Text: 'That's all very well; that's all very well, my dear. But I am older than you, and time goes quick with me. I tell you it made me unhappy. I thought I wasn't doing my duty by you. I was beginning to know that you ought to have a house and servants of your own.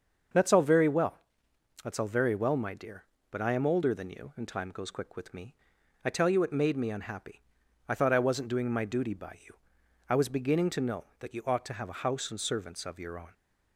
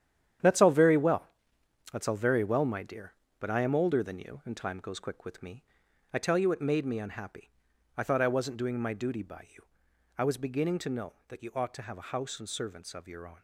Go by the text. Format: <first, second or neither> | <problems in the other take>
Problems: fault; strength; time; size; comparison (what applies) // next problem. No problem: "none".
first | gets quieter; strong; throughout; 10 dB // starts louder than the rest; strong; until 2.0 s; 9.5 dB; also in the first